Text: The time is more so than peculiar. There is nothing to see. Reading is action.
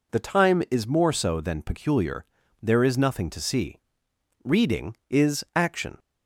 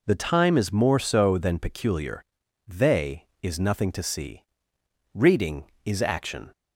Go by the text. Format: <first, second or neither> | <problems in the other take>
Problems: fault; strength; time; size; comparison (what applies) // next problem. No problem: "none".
first | says "They" for "There"; at 2.6 s